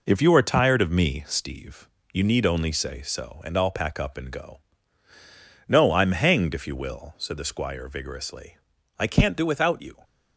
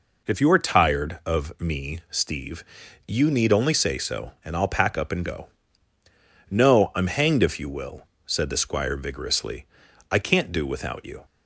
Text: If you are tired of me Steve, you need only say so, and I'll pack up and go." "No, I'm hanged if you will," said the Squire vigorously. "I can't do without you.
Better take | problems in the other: second | gets quieter; noticeable; throughout; 6 dB

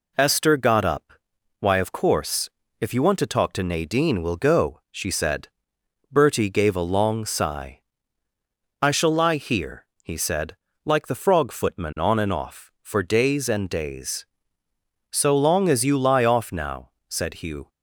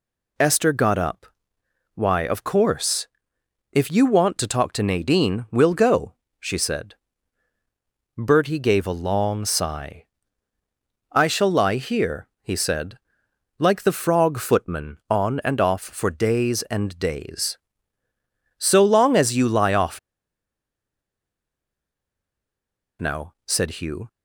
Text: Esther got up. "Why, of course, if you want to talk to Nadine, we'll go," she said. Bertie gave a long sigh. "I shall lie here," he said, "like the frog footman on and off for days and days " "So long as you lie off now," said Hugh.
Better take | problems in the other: first | pauses between "off" and "now"; strong; at 19.9 s; 3.0 s long

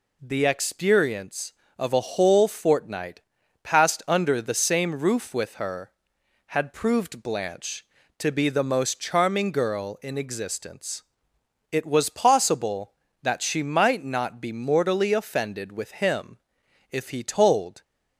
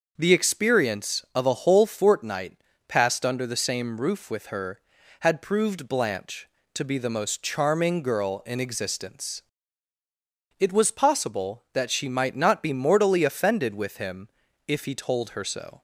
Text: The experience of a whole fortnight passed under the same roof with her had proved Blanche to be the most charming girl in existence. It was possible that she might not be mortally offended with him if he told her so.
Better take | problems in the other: second | pauses between "fortnight" and "passed"; at 3.2 s; 0.42 s long; slight in the second // pauses between "him" and "if"; noticeable; at 16.3 s; 0.54 s long; also in the second // stops before "her so"; at 17.8 s

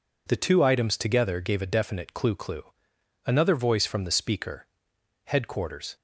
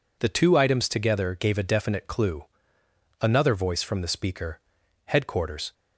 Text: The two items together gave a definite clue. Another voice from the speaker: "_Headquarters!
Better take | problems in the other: second | says "clue" twice; at 2.3 s

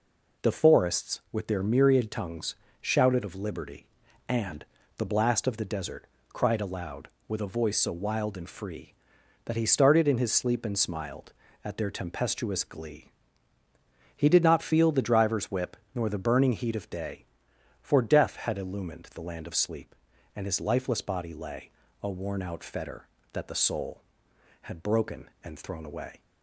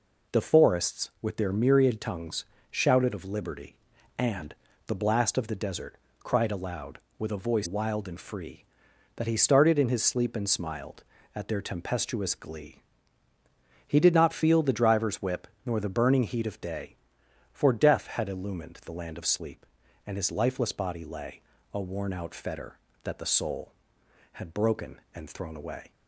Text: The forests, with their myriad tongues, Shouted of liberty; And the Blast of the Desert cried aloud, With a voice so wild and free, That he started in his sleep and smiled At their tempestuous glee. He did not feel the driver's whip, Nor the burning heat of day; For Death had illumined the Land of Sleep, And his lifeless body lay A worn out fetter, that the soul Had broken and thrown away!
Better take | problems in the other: first | pauses between "And" and "the"; slight; at 4.5 s; 0.32 s long; slight in the first // pauses between "Desert" and "cried"; slight; at 5.9 s; 0.26 s long; slight in the first // skips "so"; at 7.6 s // pauses between "lay" and "A"; slight; at 21.4 s; 0.28 s long; slight in the first

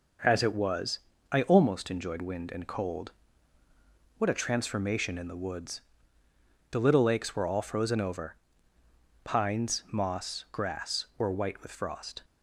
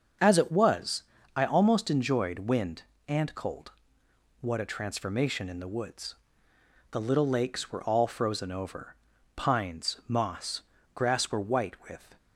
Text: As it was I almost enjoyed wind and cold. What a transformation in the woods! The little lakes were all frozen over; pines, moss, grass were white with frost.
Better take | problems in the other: first | starts louder than the rest; until 1.5 s; 7 dB // pauses between "was" and "I"; slight; at 1.0 s; 0.34 s long; slight in the first // stops before "frost"; at 12.1 s

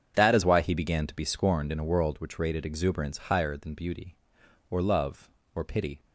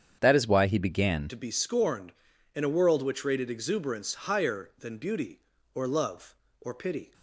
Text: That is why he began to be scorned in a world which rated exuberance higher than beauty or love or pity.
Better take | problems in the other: first | starts louder than the rest; strong; until 1.2 s; 8 dB; strong in the first // changes voice at "to"; from 1.2 s on; 5.9 s long

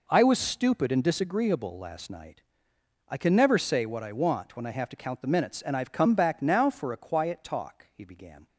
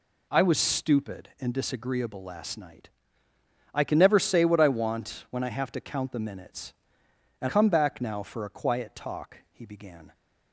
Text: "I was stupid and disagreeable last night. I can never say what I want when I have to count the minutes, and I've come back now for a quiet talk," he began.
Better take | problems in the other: first | skips "I've"; at 7.4 s

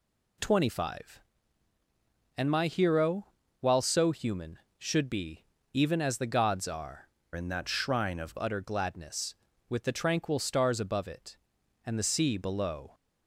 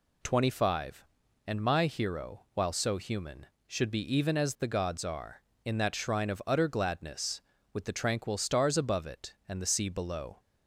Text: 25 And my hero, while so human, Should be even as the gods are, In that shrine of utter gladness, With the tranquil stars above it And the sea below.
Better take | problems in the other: second | pauses between "be" and "even"; slight; at 5.4 s; 0.26 s long // changes voice from "In" to "of"; from 7.3 to 8.3 s; 1.0 s long

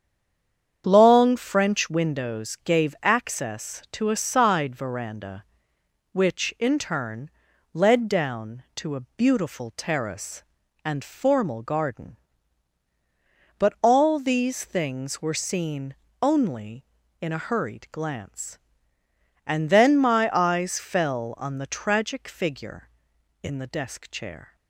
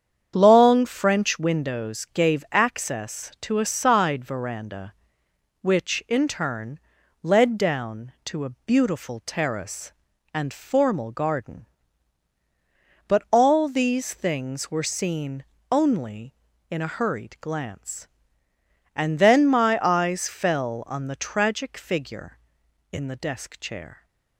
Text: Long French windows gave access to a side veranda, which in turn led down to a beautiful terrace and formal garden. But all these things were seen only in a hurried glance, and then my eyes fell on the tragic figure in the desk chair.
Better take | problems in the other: second | stays silent before the first word; slight; until 0.8 s; 0.8 s long // starts louder than the rest; strong; until 1.8 s; 8 dB; strong in the second // pauses between "turn" and "led"; at 7.3 s; 0.42 s long; also in the second // pauses between "a" and "beautiful"; slight; at 8.9 s; 0.18 s long; slight in the second // pauses between "seen" and "only"; slight; at 15.9 s; 0.26 s long; slight in the second

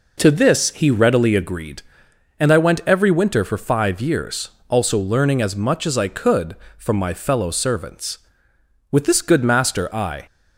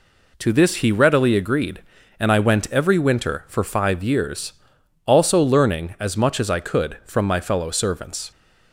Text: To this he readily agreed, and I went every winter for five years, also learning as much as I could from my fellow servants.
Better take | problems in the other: second | goes on to say "With this good master I"; from 8.9 s on; 1.3 s long

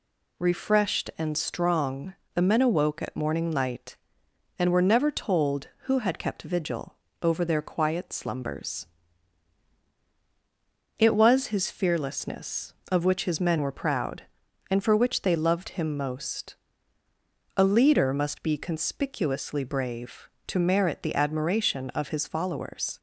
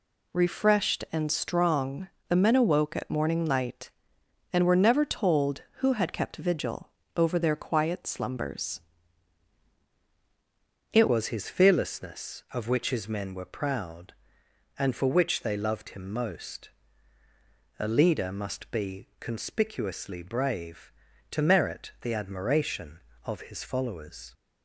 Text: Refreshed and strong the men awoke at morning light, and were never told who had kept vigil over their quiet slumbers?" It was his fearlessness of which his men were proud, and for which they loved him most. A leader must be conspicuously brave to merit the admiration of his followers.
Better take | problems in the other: first | pauses between "strong" and "the"; slight; at 2.0 s; 0.20 s long; slight in the first // pauses between "vigil" and "over"; slight; at 6.8 s; 0.26 s long; slight in the first // changes voice at "was"; from 11.0 s on; 13.3 s long

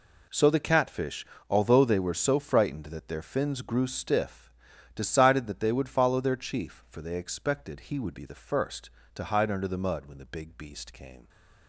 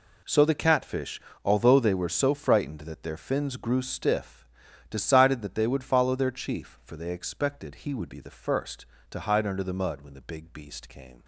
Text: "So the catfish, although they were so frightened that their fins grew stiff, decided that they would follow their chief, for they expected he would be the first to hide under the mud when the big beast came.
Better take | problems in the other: neither | none

